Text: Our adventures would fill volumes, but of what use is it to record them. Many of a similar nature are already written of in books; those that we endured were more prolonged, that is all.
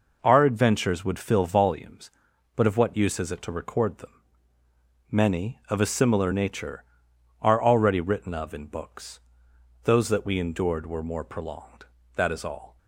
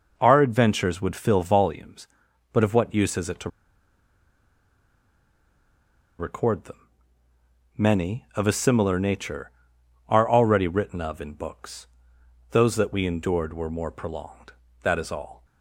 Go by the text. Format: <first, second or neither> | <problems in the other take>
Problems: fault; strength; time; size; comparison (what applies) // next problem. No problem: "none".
first | pauses between "to" and "record"; strong; at 3.4 s; 2.6 s long